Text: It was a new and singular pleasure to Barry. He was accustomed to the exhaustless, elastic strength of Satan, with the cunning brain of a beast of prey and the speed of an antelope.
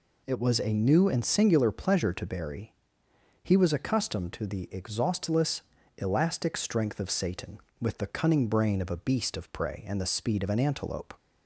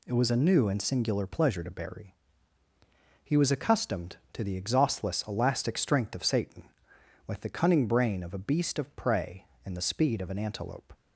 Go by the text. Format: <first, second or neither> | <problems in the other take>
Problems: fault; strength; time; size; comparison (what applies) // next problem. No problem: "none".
neither | none